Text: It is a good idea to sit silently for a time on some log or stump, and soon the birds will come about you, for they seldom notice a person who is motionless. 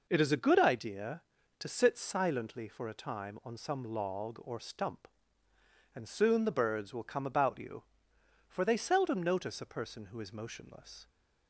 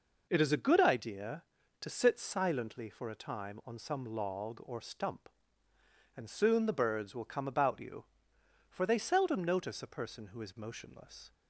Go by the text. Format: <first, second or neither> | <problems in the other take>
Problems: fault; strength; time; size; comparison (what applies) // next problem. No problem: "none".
neither | none